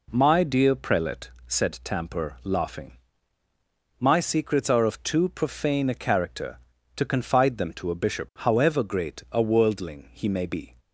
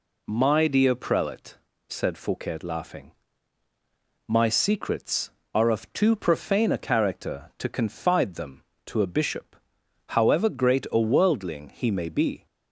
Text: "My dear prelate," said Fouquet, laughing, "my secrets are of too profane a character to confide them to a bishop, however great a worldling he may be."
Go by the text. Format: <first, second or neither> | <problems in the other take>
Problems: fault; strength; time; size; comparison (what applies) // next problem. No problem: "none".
second | says "Tamper" for "Fouquet"; at 1.8 s